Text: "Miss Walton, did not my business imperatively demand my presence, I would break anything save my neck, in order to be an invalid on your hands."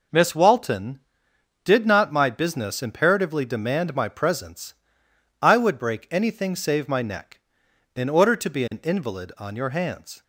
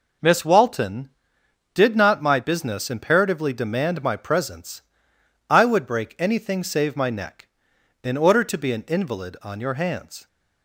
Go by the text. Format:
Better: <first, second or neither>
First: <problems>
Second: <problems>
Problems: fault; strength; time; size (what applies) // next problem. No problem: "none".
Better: neither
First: none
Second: none